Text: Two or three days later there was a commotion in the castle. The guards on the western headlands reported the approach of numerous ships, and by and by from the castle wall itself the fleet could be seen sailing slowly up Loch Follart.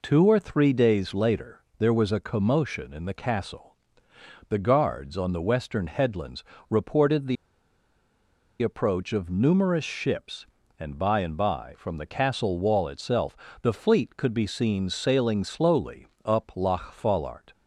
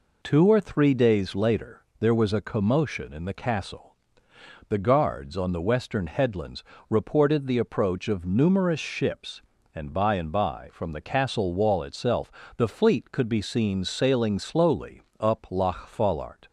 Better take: second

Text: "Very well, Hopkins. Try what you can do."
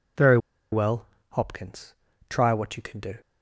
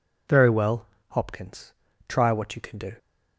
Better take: second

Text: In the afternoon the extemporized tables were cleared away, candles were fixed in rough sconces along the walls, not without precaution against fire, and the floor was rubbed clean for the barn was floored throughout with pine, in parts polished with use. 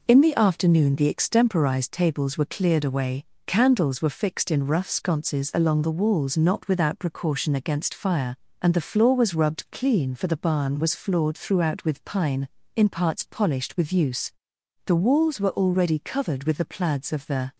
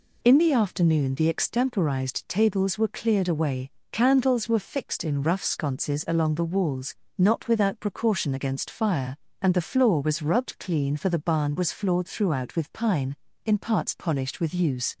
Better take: second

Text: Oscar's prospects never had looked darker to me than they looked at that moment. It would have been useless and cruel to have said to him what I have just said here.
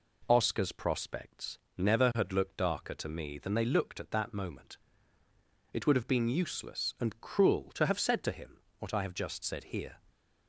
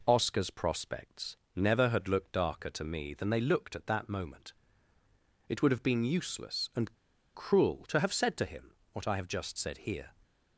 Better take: first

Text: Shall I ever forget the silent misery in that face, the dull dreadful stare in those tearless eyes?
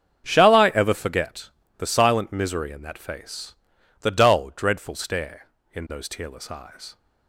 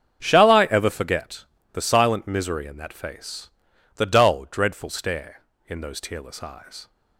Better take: neither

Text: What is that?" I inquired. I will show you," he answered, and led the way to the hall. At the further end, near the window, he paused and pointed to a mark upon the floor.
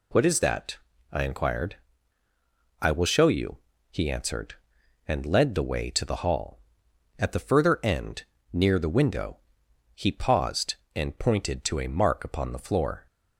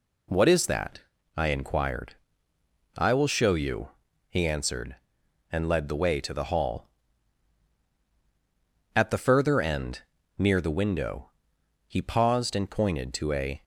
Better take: first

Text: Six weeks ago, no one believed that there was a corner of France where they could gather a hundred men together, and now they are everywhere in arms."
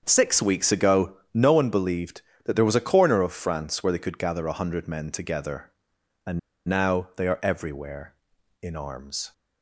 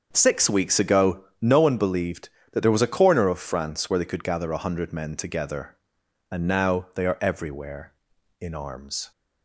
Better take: second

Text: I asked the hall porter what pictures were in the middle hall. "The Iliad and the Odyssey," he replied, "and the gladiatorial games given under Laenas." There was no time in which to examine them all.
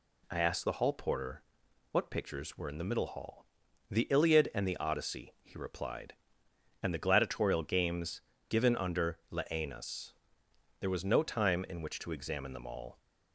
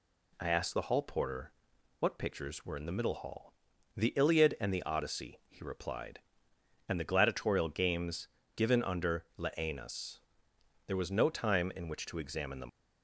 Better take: first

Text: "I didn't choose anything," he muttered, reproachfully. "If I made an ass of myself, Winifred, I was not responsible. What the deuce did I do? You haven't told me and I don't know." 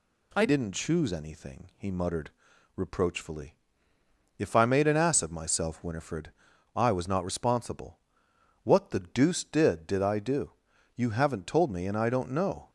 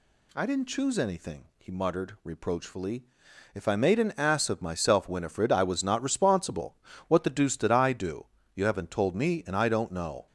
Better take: second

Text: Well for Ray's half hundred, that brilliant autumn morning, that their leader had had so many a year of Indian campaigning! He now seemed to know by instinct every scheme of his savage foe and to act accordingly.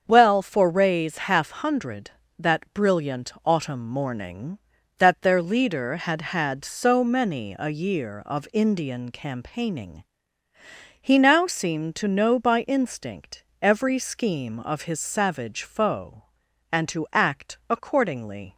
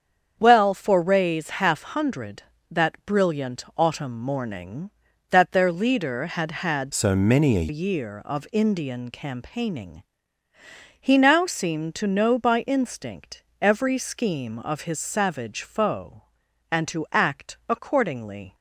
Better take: first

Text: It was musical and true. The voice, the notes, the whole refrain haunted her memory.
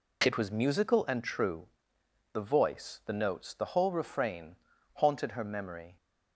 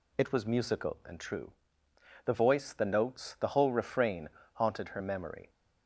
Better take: neither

